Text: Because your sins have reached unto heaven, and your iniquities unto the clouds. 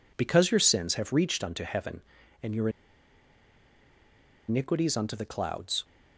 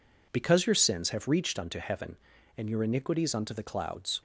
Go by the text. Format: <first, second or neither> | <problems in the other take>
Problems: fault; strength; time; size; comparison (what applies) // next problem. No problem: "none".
second | pauses between "your" and "iniquities"; strong; at 2.6 s; 1.7 s long